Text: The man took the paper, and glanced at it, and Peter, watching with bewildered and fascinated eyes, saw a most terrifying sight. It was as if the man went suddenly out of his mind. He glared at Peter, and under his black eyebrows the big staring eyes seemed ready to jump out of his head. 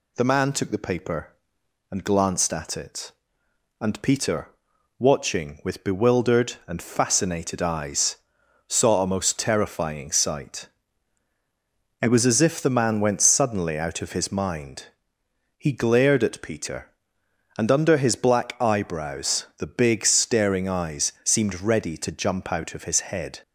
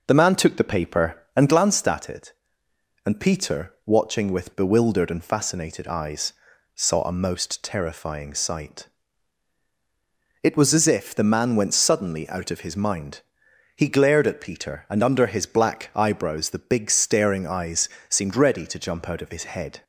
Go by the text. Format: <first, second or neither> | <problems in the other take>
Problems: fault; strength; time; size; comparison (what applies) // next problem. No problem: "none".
first | starts louder than the rest; noticeable; until 1.8 s; 5 dB // pauses between "eyes" and "seemed"; slight; at 17.8 s; 0.22 s long